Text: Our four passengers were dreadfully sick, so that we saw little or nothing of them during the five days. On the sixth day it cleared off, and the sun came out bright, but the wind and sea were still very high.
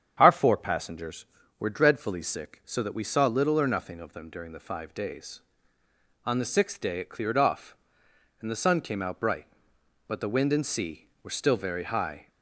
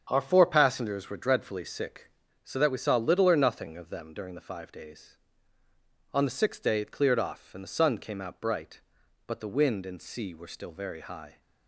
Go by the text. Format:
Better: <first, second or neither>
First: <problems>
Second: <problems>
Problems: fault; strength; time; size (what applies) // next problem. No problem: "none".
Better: neither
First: starts louder than the rest; strong; until 1.1 s; 8 dB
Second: starts louder than the rest; strong; until 1.1 s; 7.5 dB